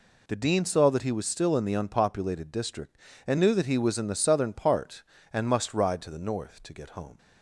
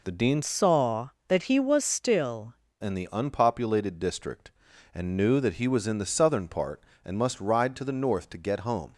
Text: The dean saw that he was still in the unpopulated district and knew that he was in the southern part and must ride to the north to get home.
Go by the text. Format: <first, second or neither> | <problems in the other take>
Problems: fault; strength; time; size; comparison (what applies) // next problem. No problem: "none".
first | changes voice from "saw" to "still"; from 0.4 to 2.5 s; 2.1 s long